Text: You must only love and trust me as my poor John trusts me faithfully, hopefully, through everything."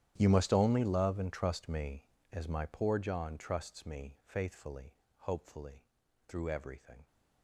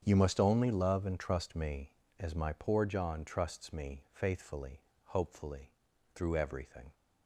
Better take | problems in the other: second | gets quieter; strong; throughout; 21 dB // starts louder than the rest; strong; until 1.1 s; 11 dB; strong in the second

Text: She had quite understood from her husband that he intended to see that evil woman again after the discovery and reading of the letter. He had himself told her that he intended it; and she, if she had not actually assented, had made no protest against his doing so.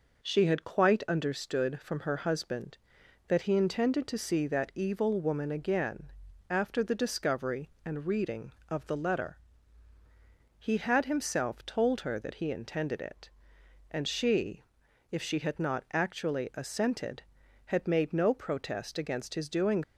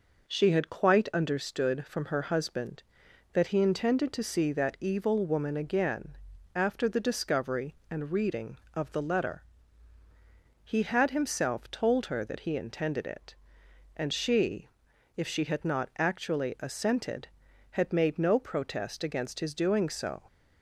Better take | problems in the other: second | pauses between "again" and "after"; slight; at 6.1 s; 0.36 s long; slight in the second // stops before "so"; at 19.8 s

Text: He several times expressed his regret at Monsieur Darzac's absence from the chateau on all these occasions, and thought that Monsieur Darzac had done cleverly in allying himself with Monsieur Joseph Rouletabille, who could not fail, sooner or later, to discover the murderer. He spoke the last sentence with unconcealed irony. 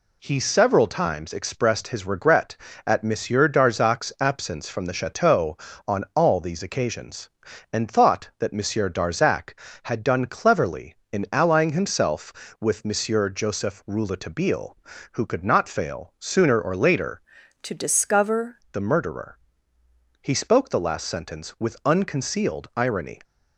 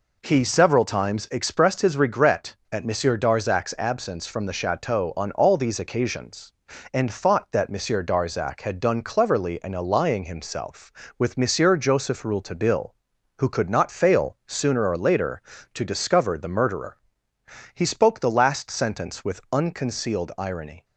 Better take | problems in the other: second | changes voice from "to" to "discover"; from 17.6 to 18.5 s; 0.9 s long

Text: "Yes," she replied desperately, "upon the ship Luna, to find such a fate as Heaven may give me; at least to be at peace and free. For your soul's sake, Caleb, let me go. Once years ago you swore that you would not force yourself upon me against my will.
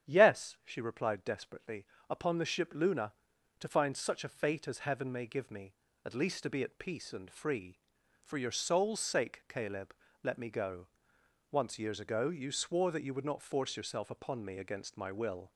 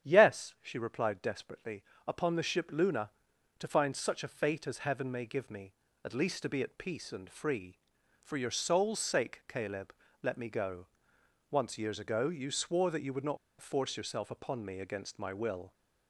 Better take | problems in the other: first | starts louder than the rest; strong; until 1.1 s; 9.5 dB; strong in the first // pauses between "not" and "force"; slight; at 13.3 s; 0.23 s long

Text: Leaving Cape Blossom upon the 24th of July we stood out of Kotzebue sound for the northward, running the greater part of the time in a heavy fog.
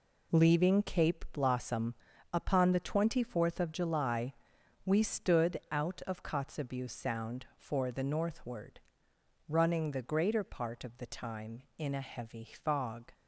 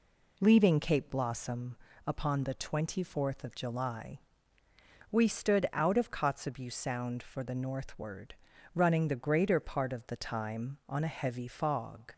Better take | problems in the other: first | pauses between "Blossom" and "upon"; slight; at 1.7 s; 0.30 s long; also in the first // pauses between "July" and "we"; noticeable; at 4.1 s; 0.92 s long; noticeable in the first // says "on" for "in"; at 10.8 s

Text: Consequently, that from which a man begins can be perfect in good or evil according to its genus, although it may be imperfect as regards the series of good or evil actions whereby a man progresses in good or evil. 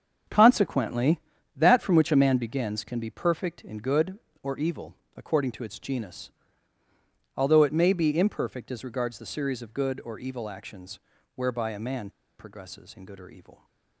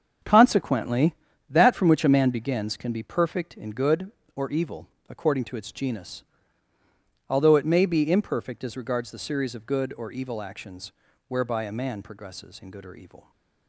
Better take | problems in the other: second | starts louder than the rest; strong; until 1.6 s; 7.5 dB; strong in the second // pauses between "evil" and "according"; slight; at 4.9 s; 0.22 s long; slight in the second // pauses between "actions" and "whereby"; slight; at 10.9 s; 0.36 s long; slight in the second // pauses between "man" and "progresses"; slight; at 12.0 s; 0.29 s long

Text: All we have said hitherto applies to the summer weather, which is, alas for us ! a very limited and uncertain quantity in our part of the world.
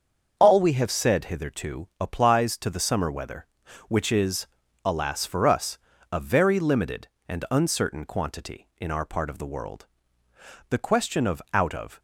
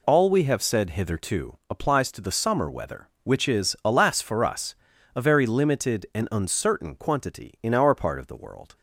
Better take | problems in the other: second | starts louder than the rest; until 1.3 s; 6.5 dB // goes on to say "The question of out of"; noticeable; from 10.6 s on; 1.3 s long

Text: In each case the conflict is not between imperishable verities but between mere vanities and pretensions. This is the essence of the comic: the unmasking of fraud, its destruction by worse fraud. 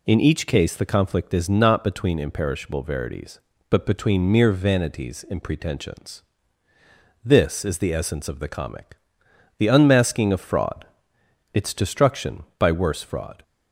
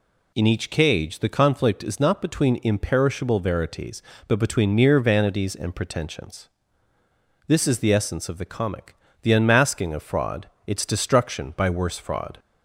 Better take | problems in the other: first | says "cage" for "case"; at 0.7 s

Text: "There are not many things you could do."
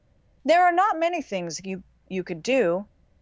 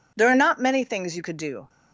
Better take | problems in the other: second | says "you" twice; at 2.0 s

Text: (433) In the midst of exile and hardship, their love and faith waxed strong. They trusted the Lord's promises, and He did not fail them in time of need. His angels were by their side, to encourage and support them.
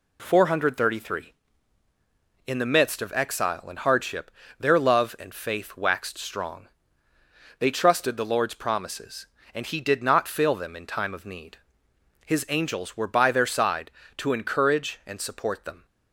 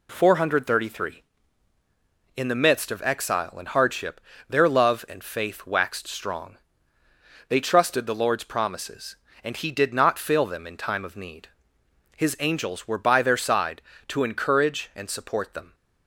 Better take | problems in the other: neither | none

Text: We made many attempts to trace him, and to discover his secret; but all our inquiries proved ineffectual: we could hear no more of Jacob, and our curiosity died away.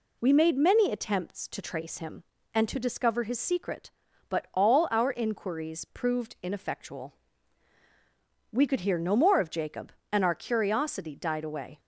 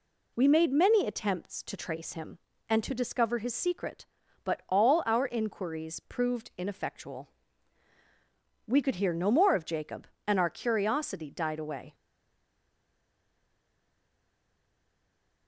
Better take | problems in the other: first | stays silent after the last word; strong; from 11.9 s on; 3.5 s long

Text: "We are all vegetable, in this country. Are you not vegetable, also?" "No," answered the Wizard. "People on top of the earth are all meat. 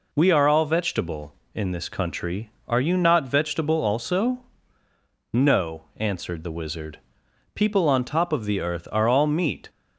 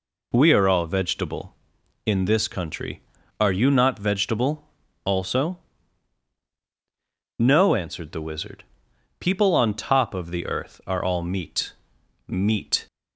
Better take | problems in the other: first | says "meat" twice; at 12.2 s

